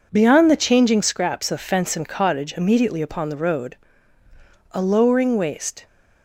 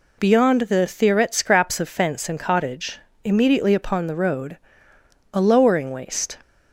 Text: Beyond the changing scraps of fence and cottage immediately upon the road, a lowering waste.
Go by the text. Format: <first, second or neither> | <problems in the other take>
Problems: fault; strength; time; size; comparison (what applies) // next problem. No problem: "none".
first | says "theoret" for "changing"; at 0.8 s // pauses between "cottage" and "immediately"; slight; at 2.9 s; 0.26 s long